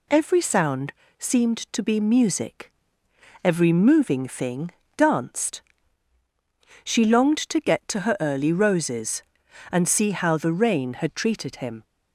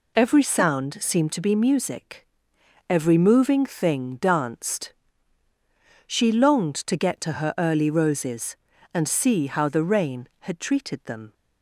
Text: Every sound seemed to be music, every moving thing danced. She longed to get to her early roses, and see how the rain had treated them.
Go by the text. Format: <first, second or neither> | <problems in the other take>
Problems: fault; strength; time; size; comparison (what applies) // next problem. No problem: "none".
second | pauses between "sound" and "seemed"; slight; at 0.9 s; 0.28 s long // pauses between "thing" and "danced"; slight; at 4.7 s; 0.26 s long // says "him" for "them"; at 11.5 s